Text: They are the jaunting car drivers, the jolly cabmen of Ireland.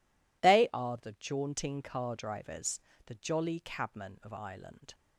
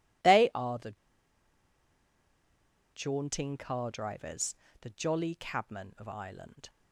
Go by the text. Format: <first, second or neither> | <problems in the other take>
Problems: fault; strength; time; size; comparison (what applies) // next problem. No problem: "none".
first | pauses between "the" and "jaunting"; strong; at 0.9 s; 1.9 s long